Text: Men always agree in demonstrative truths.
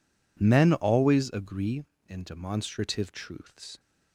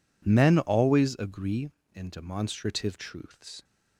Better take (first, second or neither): neither